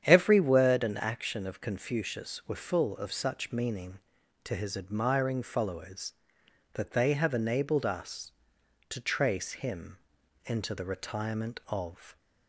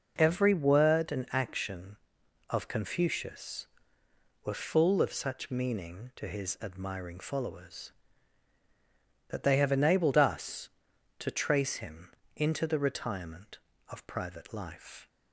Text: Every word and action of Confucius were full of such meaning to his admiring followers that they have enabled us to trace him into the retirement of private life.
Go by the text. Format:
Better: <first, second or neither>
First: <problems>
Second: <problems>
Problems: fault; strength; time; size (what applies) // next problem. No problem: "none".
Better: second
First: starts louder than the rest; strong; until 1.0 s; 9 dB // pauses between "him" and "into"; noticeable; at 9.9 s; 0.48 s long // stops before "private life"; at 12.1 s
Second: pauses between "him" and "into"; slight; at 12.0 s; 0.26 s long